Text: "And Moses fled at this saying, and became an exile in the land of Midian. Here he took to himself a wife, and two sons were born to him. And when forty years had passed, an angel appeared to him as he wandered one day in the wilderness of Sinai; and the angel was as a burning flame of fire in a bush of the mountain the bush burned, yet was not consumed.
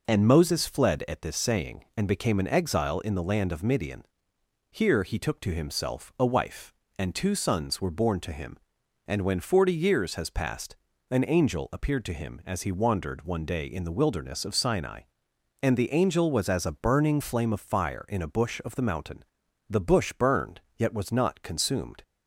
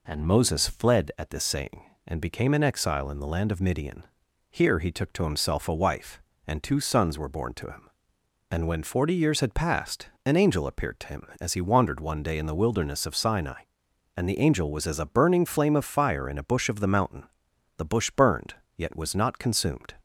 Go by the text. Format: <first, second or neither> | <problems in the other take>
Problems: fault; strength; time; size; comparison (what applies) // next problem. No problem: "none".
second | says "has" for "had"; at 10.1 s // pauses between "mountain" and "the"; noticeable; at 19.2 s; 0.46 s long; noticeable in the second